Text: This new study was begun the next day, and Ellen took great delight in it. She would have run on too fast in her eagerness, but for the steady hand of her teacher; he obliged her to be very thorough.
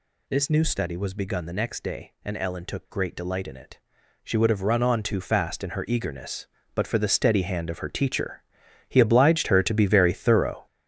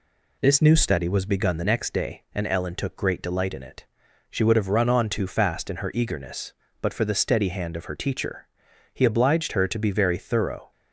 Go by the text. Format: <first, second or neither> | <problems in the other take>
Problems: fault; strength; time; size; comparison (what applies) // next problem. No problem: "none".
second | gets louder; strong; throughout; 7.5 dB